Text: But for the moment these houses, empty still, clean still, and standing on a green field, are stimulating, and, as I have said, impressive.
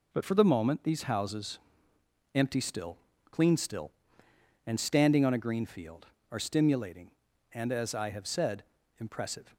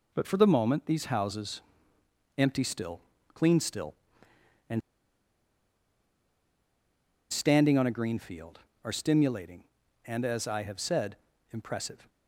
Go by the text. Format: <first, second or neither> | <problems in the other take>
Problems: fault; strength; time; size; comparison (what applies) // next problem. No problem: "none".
first | pauses between "and" and "standing"; strong; at 4.8 s; 2.5 s long